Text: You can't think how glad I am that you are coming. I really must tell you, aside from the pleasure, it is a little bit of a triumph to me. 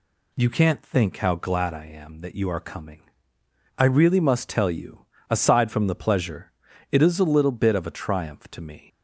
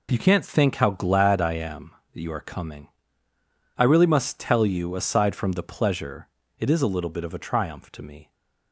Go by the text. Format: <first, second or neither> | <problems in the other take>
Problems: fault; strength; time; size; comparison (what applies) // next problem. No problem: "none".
neither | none